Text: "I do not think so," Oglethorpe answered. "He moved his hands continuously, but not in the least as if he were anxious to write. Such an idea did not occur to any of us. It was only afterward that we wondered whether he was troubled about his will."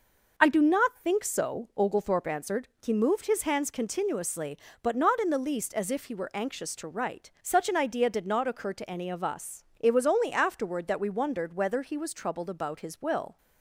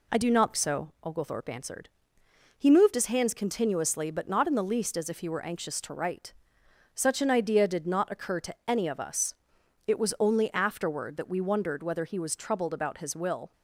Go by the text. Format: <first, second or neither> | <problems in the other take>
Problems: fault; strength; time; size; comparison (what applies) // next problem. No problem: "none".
first | skips "think"; at 0.5 s